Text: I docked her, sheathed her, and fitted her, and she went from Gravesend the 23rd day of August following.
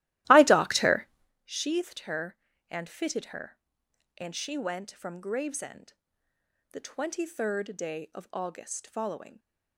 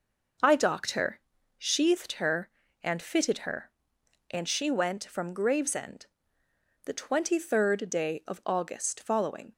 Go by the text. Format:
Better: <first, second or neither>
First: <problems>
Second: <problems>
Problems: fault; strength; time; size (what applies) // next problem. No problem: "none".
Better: second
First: starts louder than the rest; strong; until 1.3 s; 15.5 dB // pauses between "Gravesend" and "the"; noticeable; at 5.9 s; 0.78 s long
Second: pauses between "Gravesend" and "the"; noticeable; at 6.0 s; 0.78 s long